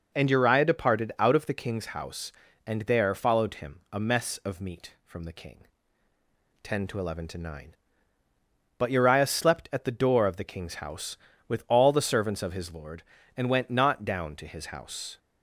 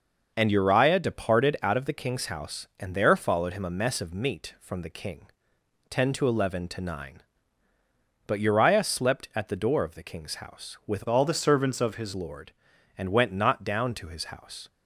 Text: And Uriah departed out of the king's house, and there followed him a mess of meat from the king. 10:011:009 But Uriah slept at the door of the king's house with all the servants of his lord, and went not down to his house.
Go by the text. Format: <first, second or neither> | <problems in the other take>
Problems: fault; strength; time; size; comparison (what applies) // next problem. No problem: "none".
first | changes voice from "all" to "his"; from 11.0 to 12.1 s; 1.1 s long